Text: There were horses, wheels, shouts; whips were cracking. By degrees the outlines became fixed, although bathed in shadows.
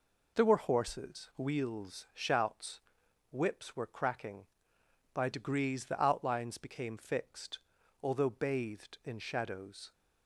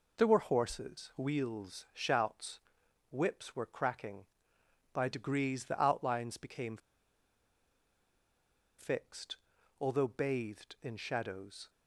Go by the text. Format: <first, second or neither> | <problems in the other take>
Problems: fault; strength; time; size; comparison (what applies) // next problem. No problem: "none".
first | pauses between "became" and "fixed"; strong; at 6.7 s; 2.0 s long